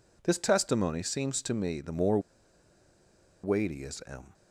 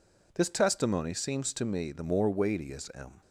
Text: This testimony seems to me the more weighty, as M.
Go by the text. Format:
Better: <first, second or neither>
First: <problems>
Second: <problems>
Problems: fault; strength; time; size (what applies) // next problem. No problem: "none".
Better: second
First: pauses between "more" and "weighty"; at 2.1 s; 1.2 s long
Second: none